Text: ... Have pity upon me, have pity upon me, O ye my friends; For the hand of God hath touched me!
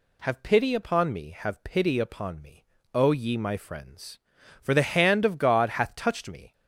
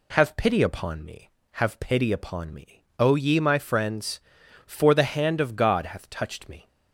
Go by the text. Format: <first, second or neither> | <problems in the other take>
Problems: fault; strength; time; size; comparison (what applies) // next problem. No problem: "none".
neither | none